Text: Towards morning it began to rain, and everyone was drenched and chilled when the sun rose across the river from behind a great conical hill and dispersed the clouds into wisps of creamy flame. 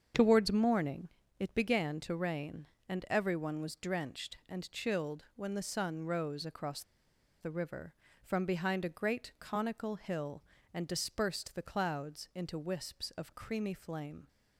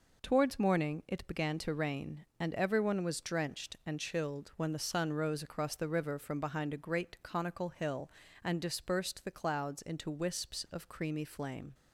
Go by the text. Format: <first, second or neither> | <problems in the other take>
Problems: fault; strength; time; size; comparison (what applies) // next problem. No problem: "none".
second | starts louder than the rest; strong; until 1.4 s; 7 dB // pauses between "morning" and "it"; slight; at 1.0 s; 0.28 s long // pauses between "across" and "the"; noticeable; at 6.8 s; 0.59 s long